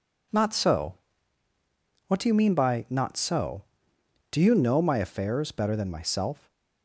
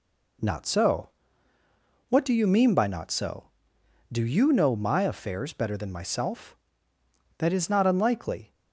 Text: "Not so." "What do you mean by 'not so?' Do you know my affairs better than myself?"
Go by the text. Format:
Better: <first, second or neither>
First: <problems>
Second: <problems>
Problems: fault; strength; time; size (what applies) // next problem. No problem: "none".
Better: first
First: none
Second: goes on to say "That is not unlikely"; noticeable; from 7.3 s on; 1.1 s long